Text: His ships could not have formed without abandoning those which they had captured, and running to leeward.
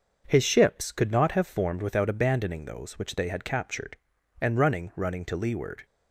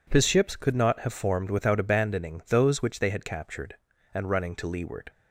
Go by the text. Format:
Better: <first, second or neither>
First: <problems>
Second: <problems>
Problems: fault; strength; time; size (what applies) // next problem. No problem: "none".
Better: second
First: starts louder than the rest; until 1.2 s; 6.5 dB // says "running" twice; at 4.9 s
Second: none